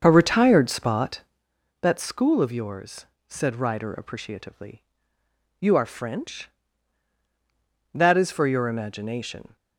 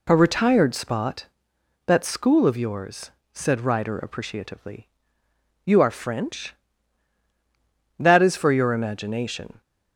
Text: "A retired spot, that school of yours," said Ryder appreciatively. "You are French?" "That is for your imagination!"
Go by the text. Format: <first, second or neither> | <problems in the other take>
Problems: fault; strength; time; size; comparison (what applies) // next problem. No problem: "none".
second | starts louder than the rest; until 1.5 s; 6.5 dB